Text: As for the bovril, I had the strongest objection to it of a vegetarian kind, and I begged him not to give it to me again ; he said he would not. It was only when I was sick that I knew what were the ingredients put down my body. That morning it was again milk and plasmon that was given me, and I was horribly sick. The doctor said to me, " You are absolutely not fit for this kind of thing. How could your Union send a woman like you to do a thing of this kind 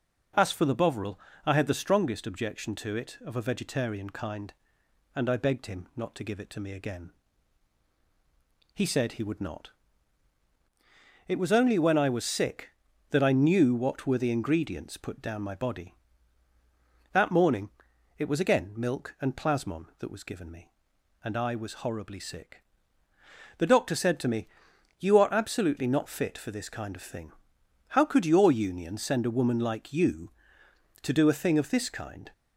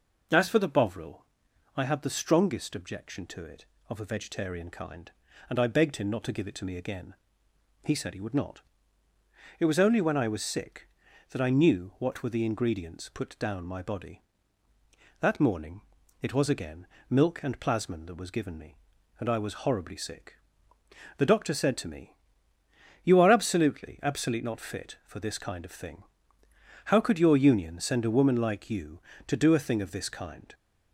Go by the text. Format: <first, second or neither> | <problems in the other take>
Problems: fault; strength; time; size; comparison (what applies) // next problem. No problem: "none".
first | pauses between "morning" and "it"; at 15.8 s; 0.40 s long; noticeable in the first // pauses between "again" and "milk"; slight; at 16.8 s; 0.24 s long // says "absolutely" twice; at 24.0 s